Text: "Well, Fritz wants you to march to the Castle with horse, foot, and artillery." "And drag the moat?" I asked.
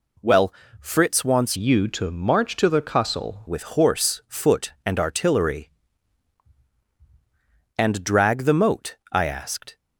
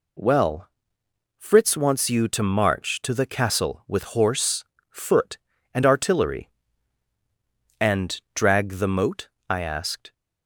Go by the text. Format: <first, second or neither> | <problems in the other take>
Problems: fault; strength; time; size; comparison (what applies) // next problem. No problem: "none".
second | changes voice from "you" to "Castle"; from 1.5 to 3.4 s; 1.9 s long